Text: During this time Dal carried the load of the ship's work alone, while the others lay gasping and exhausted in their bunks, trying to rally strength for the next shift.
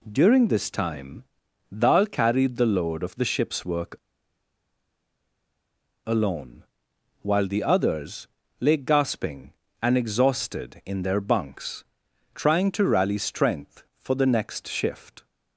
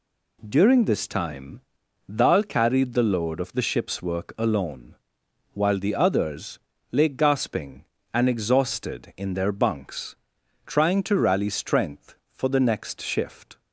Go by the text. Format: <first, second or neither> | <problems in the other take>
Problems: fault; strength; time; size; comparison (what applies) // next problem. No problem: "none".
second | pauses between "time" and "Dal"; noticeable; at 1.2 s; 0.52 s long; noticeable in the second // pauses between "work" and "alone"; strong; at 3.9 s; 2.0 s long // pauses between "others" and "lay"; slight; at 8.2 s; 0.32 s long; slight in the second